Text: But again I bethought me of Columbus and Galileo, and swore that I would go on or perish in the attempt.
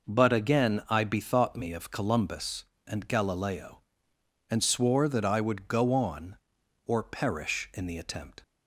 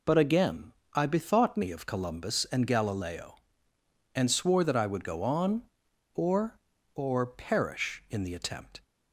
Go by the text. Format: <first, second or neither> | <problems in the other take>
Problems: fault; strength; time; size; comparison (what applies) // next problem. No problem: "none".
first | pauses between "again" and "I"; slight; at 0.7 s; 0.20 s long // says "or" twice; at 6.9 s